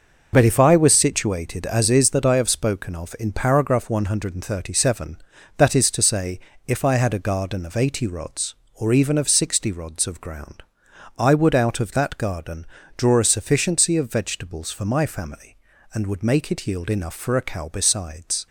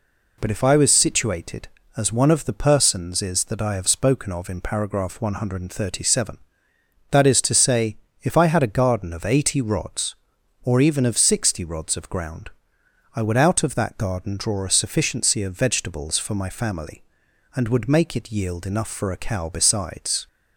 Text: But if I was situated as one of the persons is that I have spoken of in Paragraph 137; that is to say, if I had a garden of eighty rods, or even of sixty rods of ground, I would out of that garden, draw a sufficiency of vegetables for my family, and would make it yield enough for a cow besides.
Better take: second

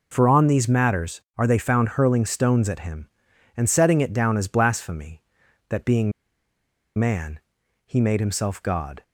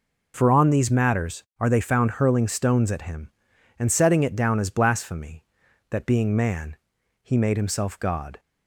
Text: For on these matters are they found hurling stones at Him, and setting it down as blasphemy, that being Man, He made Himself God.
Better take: second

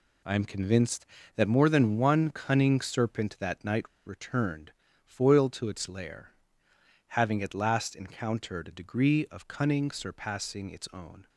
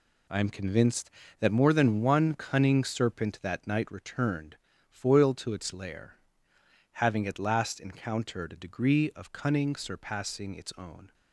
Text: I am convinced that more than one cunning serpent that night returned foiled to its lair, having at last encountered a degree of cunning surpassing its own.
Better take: second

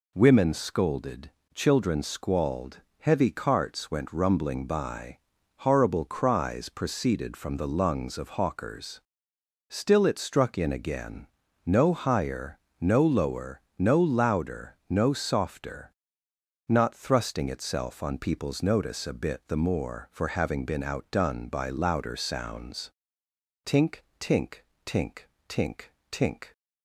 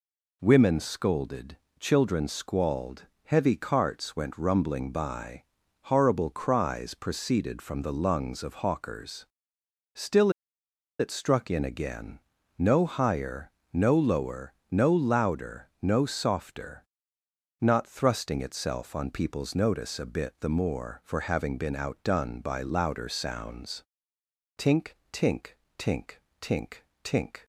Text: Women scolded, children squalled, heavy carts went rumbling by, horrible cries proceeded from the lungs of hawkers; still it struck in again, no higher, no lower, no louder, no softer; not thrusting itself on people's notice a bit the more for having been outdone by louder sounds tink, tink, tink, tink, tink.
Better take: first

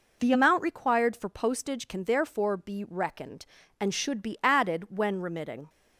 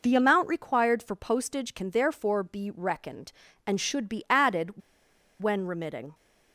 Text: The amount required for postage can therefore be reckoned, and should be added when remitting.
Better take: first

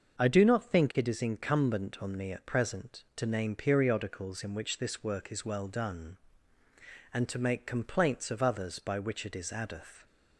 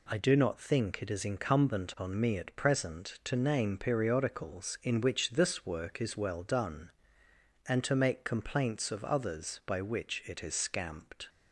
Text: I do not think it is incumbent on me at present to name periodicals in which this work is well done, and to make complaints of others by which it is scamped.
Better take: second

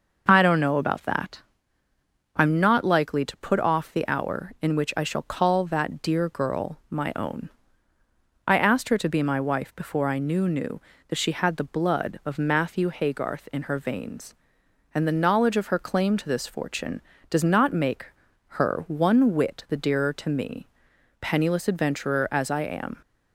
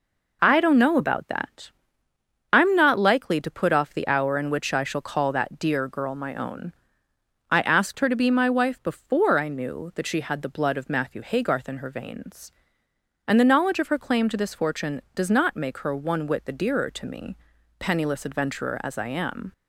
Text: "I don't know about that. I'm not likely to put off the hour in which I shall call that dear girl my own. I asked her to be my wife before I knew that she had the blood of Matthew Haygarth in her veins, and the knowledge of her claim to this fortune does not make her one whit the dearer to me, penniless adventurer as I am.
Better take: second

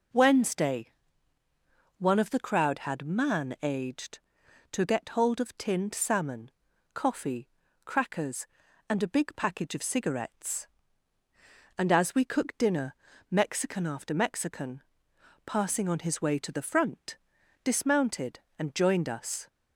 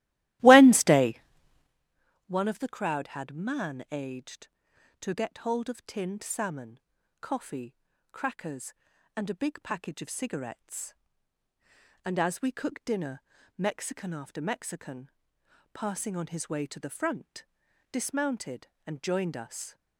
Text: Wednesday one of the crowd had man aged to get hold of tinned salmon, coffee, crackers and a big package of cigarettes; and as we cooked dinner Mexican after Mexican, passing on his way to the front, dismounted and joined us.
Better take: first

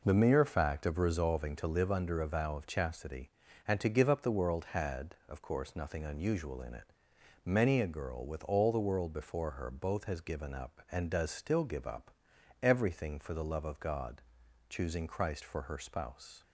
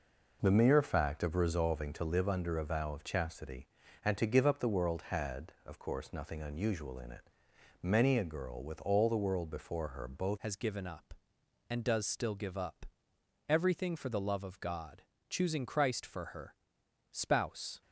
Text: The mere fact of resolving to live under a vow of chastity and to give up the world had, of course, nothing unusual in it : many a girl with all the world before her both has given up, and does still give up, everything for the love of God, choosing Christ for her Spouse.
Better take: first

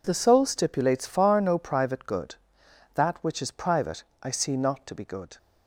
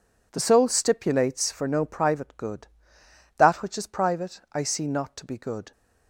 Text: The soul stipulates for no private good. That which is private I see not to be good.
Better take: second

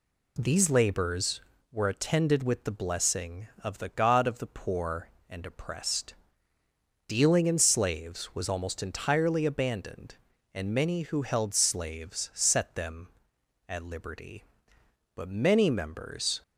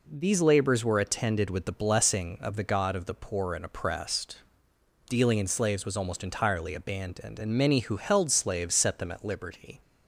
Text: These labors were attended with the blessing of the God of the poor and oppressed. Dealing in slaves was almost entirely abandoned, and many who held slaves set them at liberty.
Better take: second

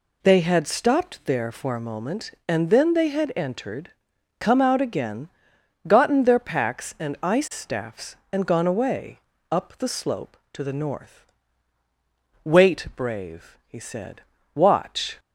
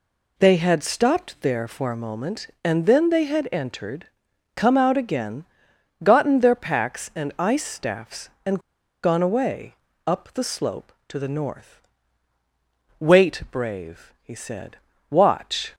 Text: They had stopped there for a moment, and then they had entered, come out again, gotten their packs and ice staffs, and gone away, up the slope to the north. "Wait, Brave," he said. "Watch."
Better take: first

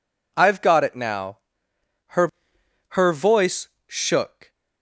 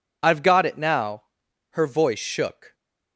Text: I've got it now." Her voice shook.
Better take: second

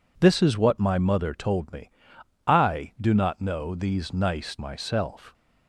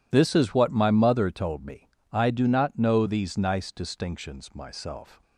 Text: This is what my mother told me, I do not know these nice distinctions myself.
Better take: second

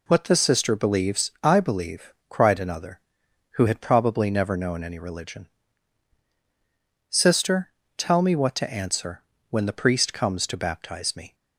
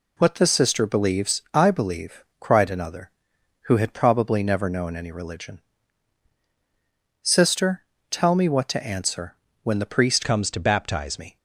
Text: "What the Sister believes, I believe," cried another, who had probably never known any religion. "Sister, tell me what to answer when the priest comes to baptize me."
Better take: first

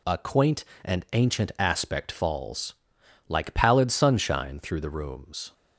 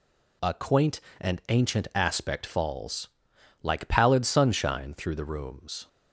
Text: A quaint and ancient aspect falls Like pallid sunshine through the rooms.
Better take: neither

